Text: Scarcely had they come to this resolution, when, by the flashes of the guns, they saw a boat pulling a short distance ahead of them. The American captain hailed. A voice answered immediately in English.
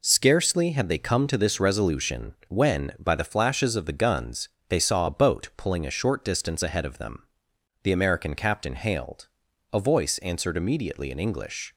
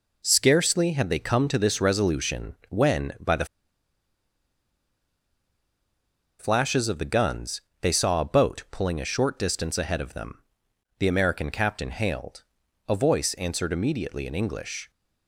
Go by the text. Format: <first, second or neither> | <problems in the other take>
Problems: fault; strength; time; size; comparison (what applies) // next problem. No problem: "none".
first | pauses between "the" and "flashes"; strong; at 3.4 s; 2.9 s long